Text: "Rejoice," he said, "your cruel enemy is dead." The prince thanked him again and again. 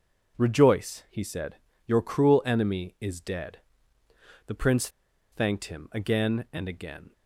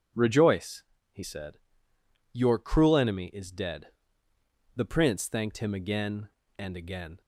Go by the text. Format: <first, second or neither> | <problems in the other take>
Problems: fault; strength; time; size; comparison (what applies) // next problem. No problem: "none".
second | pauses between "prince" and "thanked"; at 4.8 s; 0.43 s long